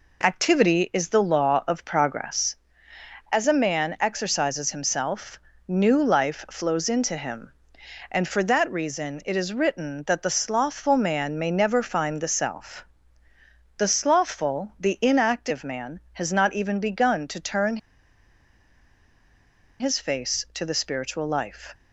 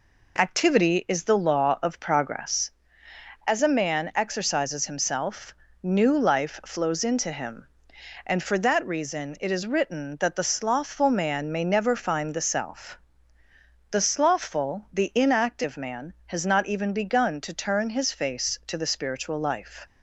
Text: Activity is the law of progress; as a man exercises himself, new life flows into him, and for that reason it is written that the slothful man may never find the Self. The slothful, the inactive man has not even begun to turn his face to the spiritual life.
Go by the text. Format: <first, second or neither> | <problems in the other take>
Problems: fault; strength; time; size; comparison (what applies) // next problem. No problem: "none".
second | pauses between "turn" and "his"; strong; at 17.7 s; 2.0 s long